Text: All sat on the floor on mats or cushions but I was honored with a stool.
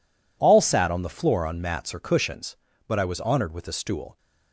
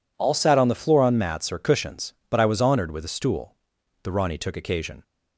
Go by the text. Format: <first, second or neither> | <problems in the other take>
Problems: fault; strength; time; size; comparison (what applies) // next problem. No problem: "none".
first | goes on to say "The Rani took occasion"; noticeable; from 4.0 s on; 0.98 s long